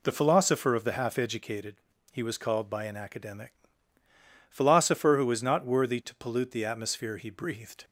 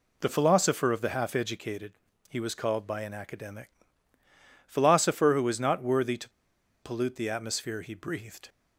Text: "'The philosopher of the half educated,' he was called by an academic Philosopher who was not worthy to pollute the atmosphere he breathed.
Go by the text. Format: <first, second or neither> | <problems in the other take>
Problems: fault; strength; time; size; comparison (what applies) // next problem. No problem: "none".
first | pauses between "academic" and "Philosopher"; noticeable; at 3.6 s; 0.98 s long; noticeable in the first // pauses between "to" and "pollute"; noticeable; at 6.2 s; 0.53 s long